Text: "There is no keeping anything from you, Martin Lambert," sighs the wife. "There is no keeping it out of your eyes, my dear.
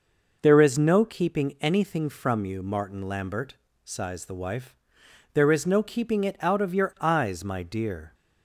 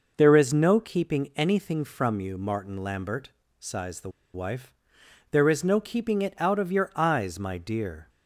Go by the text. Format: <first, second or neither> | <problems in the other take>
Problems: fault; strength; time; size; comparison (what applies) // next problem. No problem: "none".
first | pauses between "the" and "wife"; slight; at 4.1 s; 0.25 s long